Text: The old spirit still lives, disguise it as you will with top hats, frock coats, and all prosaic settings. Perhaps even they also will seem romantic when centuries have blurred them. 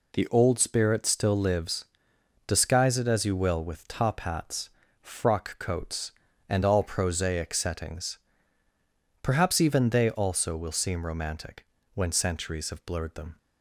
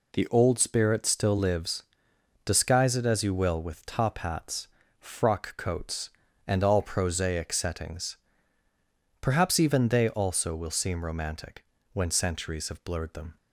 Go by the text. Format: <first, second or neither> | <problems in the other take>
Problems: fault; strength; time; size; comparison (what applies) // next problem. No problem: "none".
neither | pauses between "romantic" and "when"; slight; the same in both